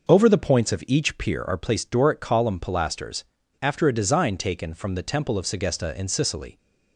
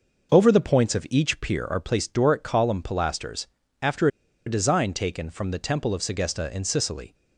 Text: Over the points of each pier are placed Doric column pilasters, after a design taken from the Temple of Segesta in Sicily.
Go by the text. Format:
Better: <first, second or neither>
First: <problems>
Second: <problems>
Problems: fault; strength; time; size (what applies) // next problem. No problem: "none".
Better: first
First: none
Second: pauses between "after" and "a"; at 4.0 s; 0.39 s long